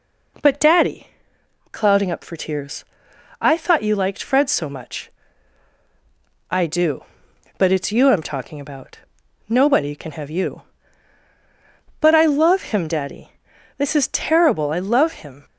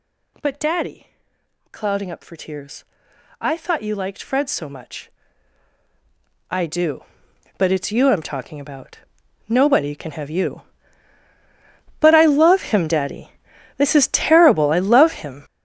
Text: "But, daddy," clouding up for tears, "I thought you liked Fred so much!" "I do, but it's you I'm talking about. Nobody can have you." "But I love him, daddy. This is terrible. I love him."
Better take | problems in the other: first | gets louder; strong; throughout; 12.5 dB

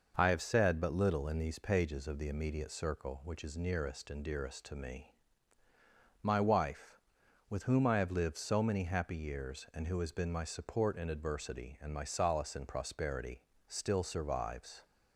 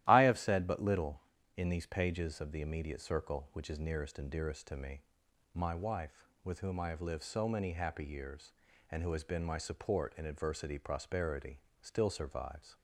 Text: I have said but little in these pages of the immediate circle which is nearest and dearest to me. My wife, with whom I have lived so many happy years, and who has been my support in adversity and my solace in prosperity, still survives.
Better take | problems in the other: first | starts louder than the rest; strong; until 1.0 s; 13.5 dB // skips "and my solace in"; at 10.7 s

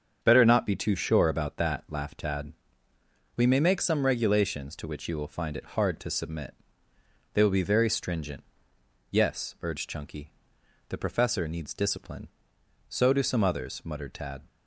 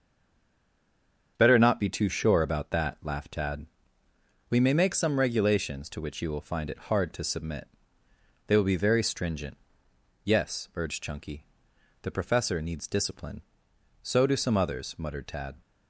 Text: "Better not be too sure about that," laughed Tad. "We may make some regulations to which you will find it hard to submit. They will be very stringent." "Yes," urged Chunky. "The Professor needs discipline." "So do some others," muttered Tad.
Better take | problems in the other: first | stays silent before the first word; noticeable; until 1.3 s; 1.3 s long // starts louder than the rest; until 2.3 s; 7 dB; also in the first

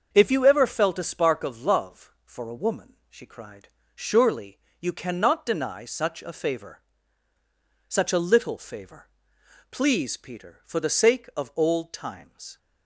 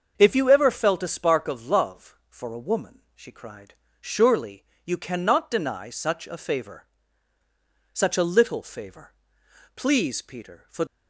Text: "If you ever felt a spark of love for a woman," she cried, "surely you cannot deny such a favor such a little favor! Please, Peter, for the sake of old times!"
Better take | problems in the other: first | starts louder than the rest; until 1.1 s; 6.5 dB; also in the first // pauses between "surely" and "you"; slight; at 4.6 s; 0.21 s long; slight in the first // pauses between "favor" and "such"; at 6.8 s; 1.0 s long; also in the first // stops before "the sake of old times"; at 10.8 s

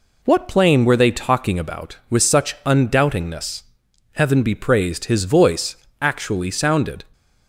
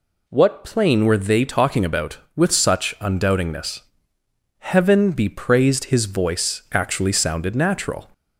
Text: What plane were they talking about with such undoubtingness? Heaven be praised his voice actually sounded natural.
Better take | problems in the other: second | pauses between "voice" and "actually"; slight; at 5.7 s; 0.24 s long // stops before "natural"; at 7.1 s

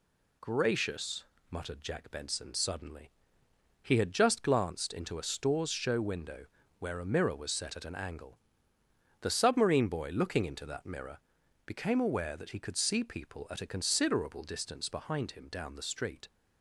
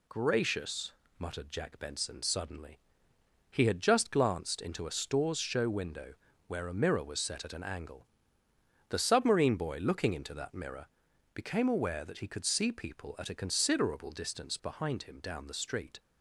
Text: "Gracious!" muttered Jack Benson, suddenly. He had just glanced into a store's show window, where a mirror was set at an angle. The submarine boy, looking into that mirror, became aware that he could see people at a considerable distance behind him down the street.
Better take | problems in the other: neither | none

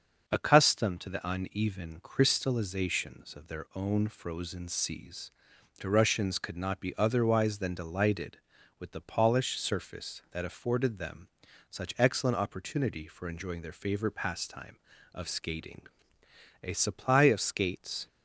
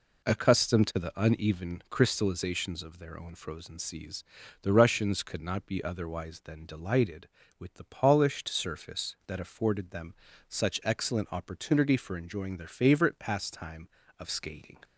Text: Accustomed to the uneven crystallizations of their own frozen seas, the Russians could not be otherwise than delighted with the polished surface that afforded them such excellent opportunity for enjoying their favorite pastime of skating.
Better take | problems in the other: second | starts louder than the rest; until 1.3 s; 6 dB // pauses between "them" and "such"; at 11.2 s; 0.42 s long; slight in the second // goes on to say "A supply of skates"; from 16.6 s on; 1.4 s long

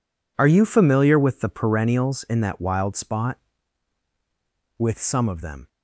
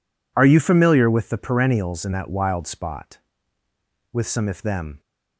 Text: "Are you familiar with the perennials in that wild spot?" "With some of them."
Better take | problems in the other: first | says "if" for "of"; at 4.4 s

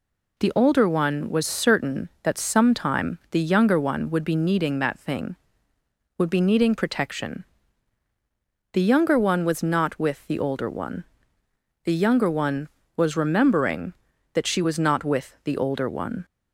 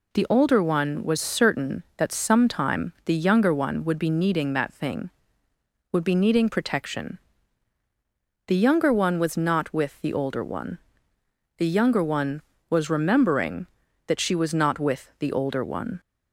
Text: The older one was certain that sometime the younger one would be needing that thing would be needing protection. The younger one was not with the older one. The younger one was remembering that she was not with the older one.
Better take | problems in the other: neither | none

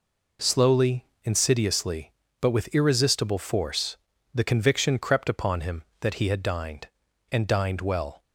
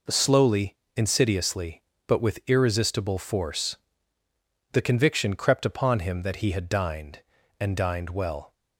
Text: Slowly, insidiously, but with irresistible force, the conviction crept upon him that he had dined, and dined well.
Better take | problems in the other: neither | none

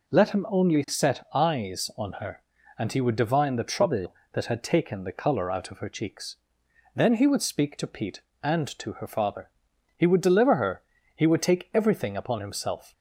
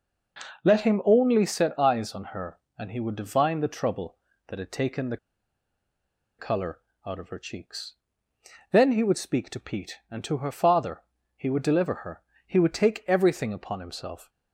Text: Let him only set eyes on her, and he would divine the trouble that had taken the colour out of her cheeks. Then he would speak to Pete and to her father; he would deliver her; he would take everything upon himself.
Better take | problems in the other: first | pauses between "the" and "colour"; at 5.1 s; 1.2 s long // pauses between "colour" and "out"; slight; at 6.8 s; 0.24 s long

